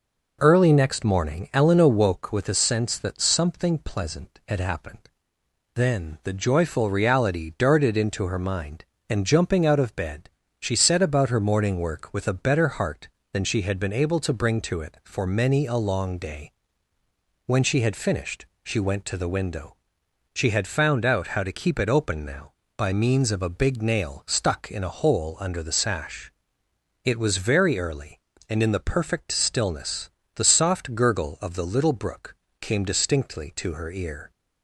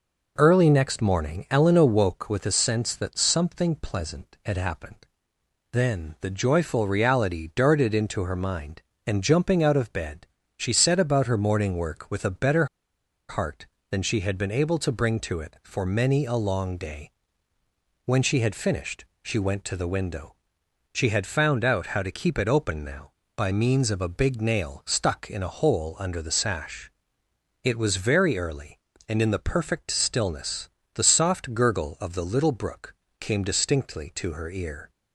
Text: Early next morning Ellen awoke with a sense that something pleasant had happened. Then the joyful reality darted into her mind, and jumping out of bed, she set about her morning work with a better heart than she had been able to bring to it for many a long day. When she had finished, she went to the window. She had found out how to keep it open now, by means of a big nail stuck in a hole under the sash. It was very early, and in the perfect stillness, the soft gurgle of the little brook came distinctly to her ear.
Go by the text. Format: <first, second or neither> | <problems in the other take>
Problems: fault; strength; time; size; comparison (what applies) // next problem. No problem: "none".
first | pauses between "better" and "heart"; noticeable; at 12.6 s; 0.62 s long // pauses between "brook" and "came"; slight; at 32.9 s; 0.24 s long; slight in the first